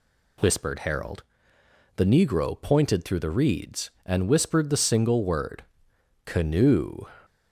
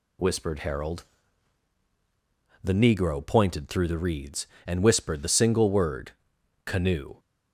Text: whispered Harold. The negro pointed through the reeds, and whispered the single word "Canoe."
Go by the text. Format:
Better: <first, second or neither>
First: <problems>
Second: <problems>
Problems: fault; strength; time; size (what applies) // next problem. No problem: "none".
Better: neither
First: pauses between "word" and "Canoe"; noticeable; at 5.6 s; 0.62 s long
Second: pauses between "word" and "Canoe"; noticeable; at 6.1 s; 0.54 s long